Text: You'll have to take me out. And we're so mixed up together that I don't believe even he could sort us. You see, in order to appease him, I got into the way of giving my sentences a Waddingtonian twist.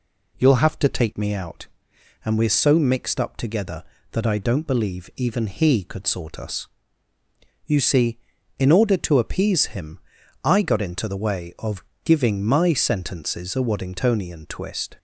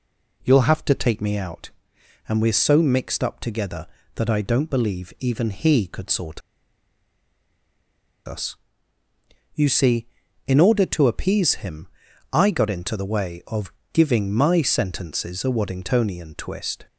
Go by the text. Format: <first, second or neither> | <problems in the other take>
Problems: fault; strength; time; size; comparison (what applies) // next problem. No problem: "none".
first | pauses between "sort" and "us"; strong; at 6.4 s; 1.8 s long // pauses between "of" and "giving"; slight; at 13.7 s; 0.20 s long; slight in the first